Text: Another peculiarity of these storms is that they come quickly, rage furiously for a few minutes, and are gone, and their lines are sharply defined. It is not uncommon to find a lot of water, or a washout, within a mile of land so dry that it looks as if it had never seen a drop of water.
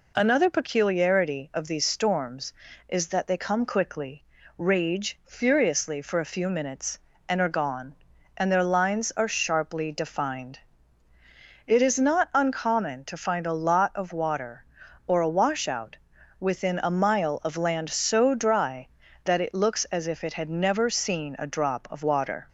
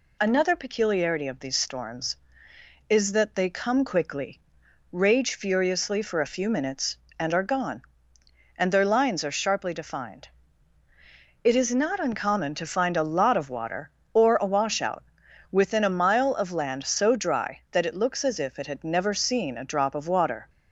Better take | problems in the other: neither | none

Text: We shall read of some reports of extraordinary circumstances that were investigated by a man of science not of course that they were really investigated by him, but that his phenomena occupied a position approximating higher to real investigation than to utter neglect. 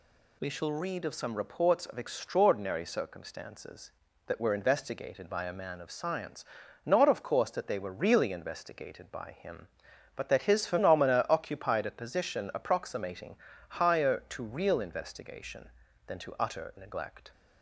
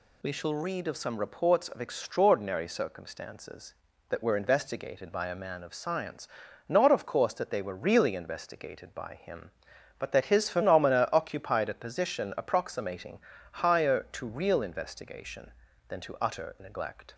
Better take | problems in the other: neither | pauses between "science" and "not"; the same in both // pauses between "approximating" and "higher"; slight; the same in both

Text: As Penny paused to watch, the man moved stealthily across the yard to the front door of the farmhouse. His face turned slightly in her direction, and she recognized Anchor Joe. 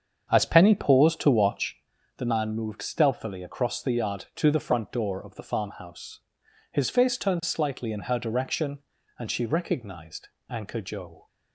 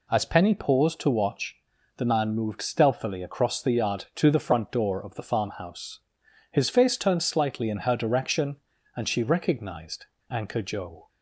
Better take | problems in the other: second | starts louder than the rest; strong; until 1.9 s; 7 dB // pauses between "recognized" and "Anchor"; slight; at 10.2 s; 0.20 s long; slight in the second

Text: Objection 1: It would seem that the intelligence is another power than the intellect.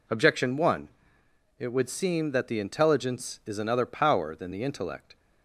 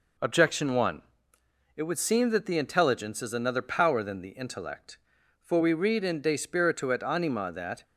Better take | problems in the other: first | goes on to say "For we read in De Spiritu et Anima that"; strong; from 5.4 s on; 2.4 s long

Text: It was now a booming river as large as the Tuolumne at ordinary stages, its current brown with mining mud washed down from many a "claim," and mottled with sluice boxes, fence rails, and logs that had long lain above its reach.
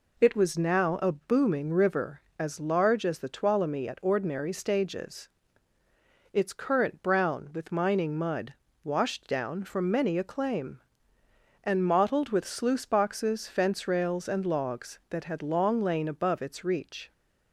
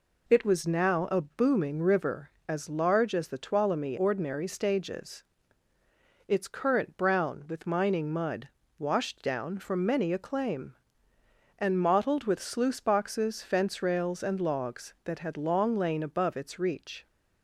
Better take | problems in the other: first | skips "at"; at 3.9 s // pauses between "mud" and "washed"; slight; at 8.4 s; 0.28 s long; slight in the first

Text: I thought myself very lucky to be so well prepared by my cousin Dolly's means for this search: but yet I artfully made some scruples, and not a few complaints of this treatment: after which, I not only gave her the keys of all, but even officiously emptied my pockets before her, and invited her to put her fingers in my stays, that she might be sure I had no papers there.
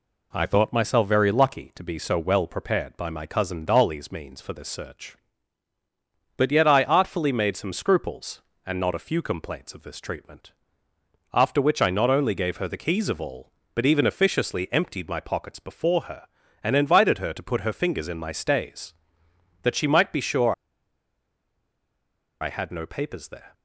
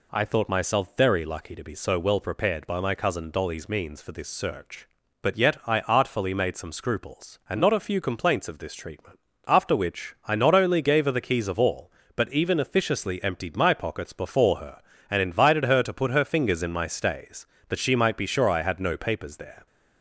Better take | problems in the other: second | pauses between "sure" and "I"; strong; at 20.5 s; 1.8 s long

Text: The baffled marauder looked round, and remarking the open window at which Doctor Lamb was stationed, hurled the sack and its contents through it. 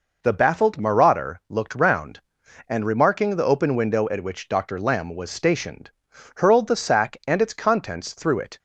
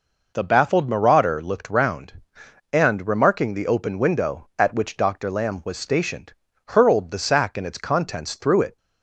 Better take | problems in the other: neither | none

